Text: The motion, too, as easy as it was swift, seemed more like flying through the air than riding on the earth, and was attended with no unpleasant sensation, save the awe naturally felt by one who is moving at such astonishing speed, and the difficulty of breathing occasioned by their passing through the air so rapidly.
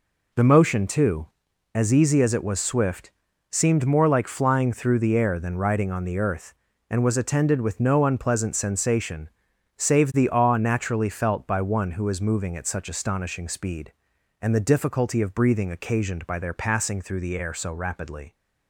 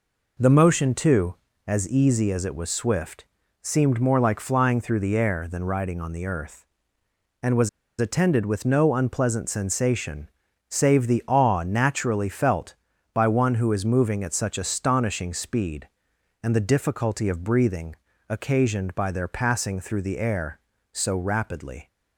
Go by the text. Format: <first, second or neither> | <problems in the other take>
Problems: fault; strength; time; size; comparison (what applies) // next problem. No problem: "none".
first | pauses between "was" and "attended"; slight; at 7.6 s; 0.31 s long // pauses between "breathing" and "occasioned"; slight; at 17.9 s; 0.32 s long